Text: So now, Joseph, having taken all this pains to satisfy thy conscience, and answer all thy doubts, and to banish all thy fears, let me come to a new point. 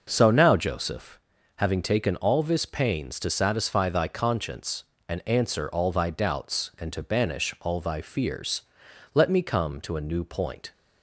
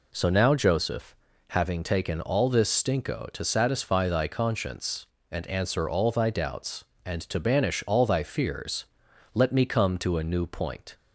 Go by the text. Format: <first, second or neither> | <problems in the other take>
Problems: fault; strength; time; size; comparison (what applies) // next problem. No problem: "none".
first | says "stinko" for "pains"; at 2.6 s